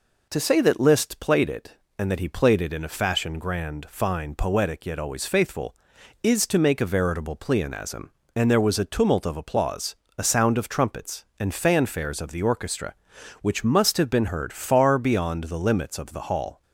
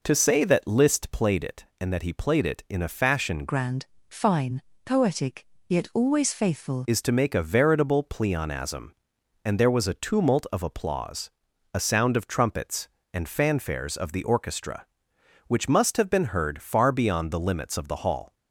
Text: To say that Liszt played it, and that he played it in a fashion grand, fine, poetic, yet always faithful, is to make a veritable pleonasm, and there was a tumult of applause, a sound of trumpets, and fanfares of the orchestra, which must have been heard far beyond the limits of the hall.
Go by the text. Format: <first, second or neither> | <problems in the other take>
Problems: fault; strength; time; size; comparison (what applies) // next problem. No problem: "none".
first | changes voice from "grand" to "faithful"; from 3.4 to 6.8 s; 3.4 s long